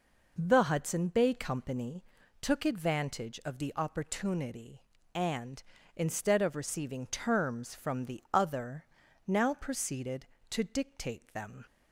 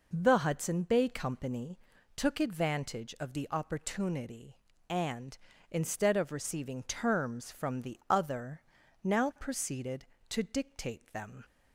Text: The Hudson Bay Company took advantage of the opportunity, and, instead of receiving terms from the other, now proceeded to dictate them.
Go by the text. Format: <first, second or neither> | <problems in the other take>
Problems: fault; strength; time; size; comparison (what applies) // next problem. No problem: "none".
neither | pauses between "Company" and "took"; the same in both